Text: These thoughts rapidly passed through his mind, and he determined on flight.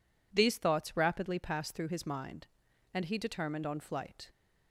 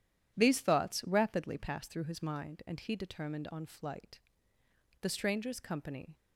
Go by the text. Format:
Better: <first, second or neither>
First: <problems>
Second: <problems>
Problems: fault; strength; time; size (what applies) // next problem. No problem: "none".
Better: first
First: none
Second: goes on to say "The stranger's company"; noticeable; from 5.0 s on; 1.1 s long